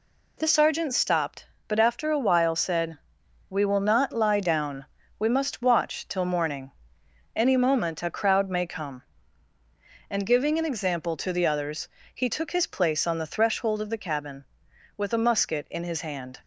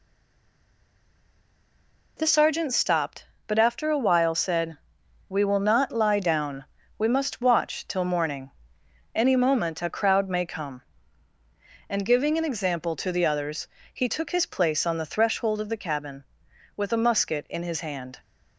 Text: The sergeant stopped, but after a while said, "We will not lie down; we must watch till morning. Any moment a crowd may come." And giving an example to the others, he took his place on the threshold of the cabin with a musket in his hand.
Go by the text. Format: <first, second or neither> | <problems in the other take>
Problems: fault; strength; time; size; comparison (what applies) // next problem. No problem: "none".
first | stays silent before the first word; until 2.1 s; 2.1 s long